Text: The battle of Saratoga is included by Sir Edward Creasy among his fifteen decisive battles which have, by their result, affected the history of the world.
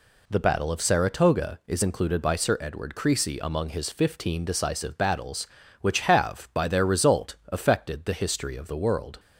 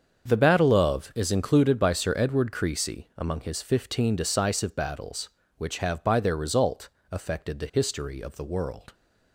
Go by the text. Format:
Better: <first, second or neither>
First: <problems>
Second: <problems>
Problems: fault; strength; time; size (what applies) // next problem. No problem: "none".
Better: first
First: none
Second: starts louder than the rest; until 1.2 s; 7 dB // skips "Saratoga"; at 1.1 s